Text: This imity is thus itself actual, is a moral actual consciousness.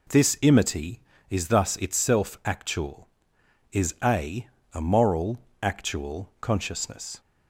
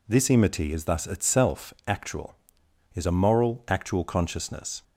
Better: second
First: says "a" twice; at 4.7 s // pauses between "moral" and "actual"; slight; at 5.3 s; 0.24 s long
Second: none

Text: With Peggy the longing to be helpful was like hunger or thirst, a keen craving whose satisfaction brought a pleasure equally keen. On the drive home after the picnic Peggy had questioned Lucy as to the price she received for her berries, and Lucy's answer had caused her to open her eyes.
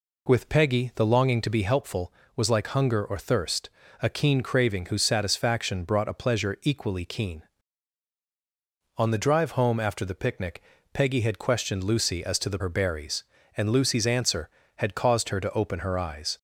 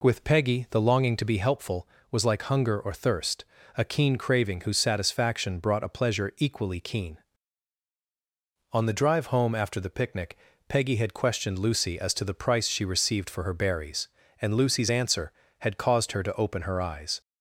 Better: second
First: pauses between "picnic" and "Peggy"; slight; at 10.6 s; 0.32 s long // skips "price she received for"; at 12.5 s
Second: pauses between "picnic" and "Peggy"; slight; at 10.3 s; 0.32 s long

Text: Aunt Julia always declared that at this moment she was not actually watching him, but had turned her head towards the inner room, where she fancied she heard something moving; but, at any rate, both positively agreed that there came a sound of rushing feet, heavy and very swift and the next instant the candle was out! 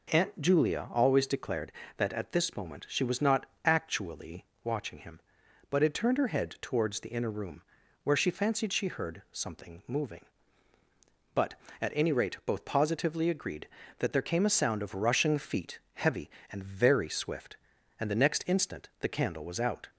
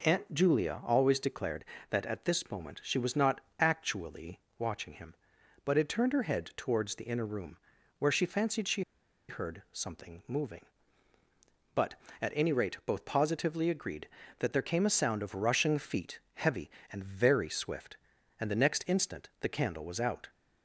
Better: first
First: pauses between "not" and "actually"; slight; at 3.4 s; 0.20 s long // pauses between "actually" and "watching"; slight; at 4.4 s; 0.18 s long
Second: pauses between "not" and "actually"; slight; at 3.3 s; 0.20 s long // pauses between "actually" and "watching"; slight; at 4.3 s; 0.18 s long // pauses between "she" and "heard"; noticeable; at 8.8 s; 0.47 s long

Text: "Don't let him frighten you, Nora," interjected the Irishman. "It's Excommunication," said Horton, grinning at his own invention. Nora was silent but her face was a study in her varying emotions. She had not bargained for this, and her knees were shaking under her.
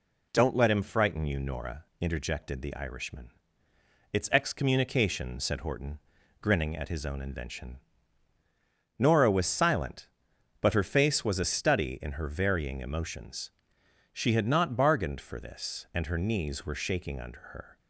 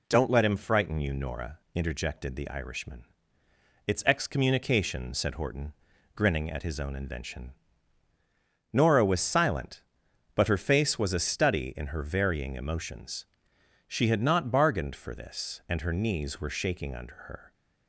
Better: neither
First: none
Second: none

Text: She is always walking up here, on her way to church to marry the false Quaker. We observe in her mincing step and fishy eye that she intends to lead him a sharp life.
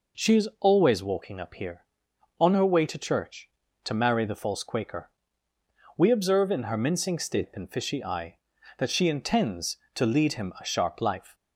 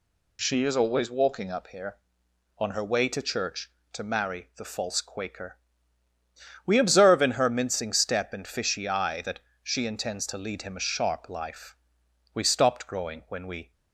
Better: first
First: none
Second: pauses between "that" and "she"; slight; at 9.4 s; 0.22 s long // goes on to say "We stopped growing when we"; from 12.3 s on; 1.3 s long

